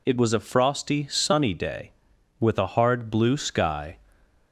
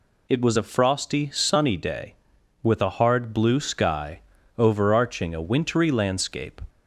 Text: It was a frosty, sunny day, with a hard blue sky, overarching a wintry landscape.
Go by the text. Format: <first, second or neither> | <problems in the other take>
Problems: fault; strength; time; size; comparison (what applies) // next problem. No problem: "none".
second | stops before "overarching a wintry landscape"; at 4.2 s